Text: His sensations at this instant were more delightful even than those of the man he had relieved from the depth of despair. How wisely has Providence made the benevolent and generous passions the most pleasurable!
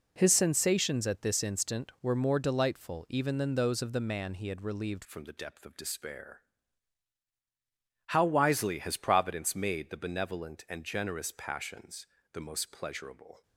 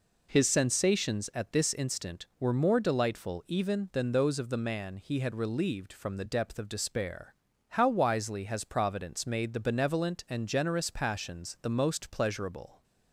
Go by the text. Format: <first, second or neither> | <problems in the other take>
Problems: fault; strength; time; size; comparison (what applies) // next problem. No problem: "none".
second | changes voice at "from"; from 5.0 s on; 8.4 s long // pauses between "passions" and "the"; slight; at 12.0 s; 0.26 s long